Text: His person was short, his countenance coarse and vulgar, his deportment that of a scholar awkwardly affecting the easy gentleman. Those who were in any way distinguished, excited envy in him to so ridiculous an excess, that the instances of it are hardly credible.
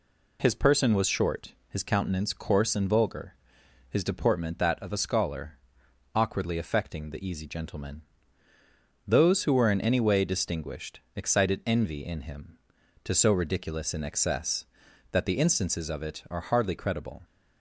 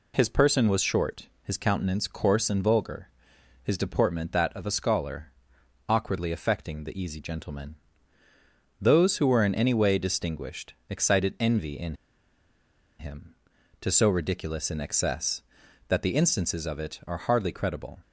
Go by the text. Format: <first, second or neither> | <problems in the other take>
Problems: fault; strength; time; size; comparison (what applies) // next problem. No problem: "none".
first | pauses between "scholar" and "awkwardly"; noticeable; at 5.3 s; 0.56 s long; noticeable in the first // pauses between "in" and "him"; at 11.9 s; 1.0 s long